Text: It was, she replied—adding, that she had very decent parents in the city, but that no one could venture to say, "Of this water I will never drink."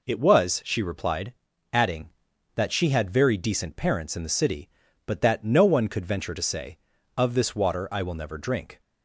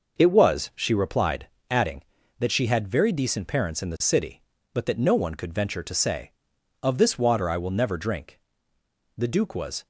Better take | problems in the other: first | goes on to say "The duke was"; noticeable; from 9.1 s on; 0.70 s long

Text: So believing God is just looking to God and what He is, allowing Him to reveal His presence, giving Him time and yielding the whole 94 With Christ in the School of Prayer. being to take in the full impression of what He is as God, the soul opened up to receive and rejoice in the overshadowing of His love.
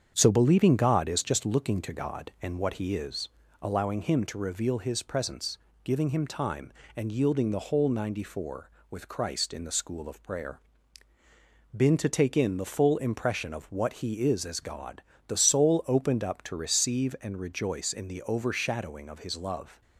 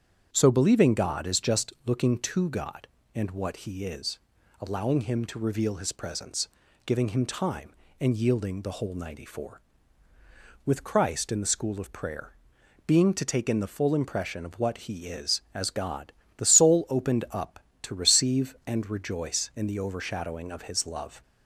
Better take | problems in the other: second | starts louder than the rest; strong; until 1.1 s; 8 dB; strong in the second // says "been" for "being"; at 11.7 s

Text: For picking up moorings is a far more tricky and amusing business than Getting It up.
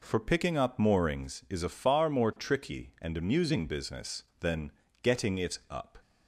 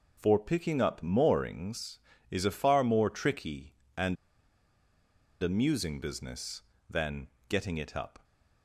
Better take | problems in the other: first | pauses between "and" and "amusing"; strong; at 4.1 s; 1.2 s long // pauses between "than" and "Getting"; slight; at 7.2 s; 0.22 s long; slight in the first

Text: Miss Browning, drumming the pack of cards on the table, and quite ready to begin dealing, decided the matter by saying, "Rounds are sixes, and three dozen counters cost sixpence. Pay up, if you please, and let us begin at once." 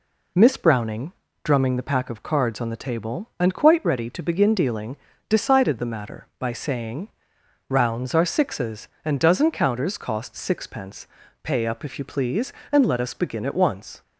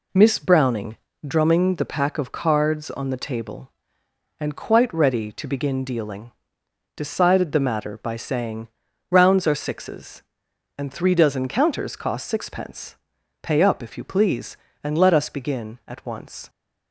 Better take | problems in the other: second | skips "three"; at 9.1 s

